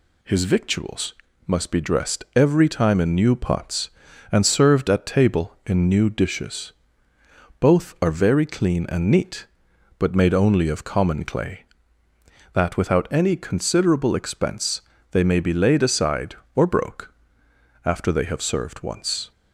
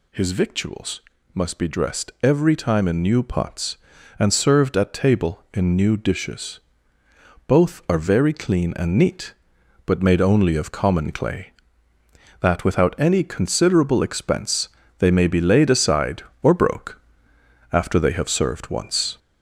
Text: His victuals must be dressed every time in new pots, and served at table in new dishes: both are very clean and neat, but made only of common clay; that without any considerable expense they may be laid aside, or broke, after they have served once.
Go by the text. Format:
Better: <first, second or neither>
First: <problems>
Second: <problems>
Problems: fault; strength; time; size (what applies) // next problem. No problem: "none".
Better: first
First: pauses between "victuals" and "must"; slight; at 1.1 s; 0.34 s long // pauses between "expense" and "they"; slight; at 14.8 s; 0.28 s long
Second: gets louder; throughout; 3.5 dB // pauses between "victuals" and "must"; slight; at 1.0 s; 0.34 s long // pauses between "expense" and "they"; slight; at 14.6 s; 0.28 s long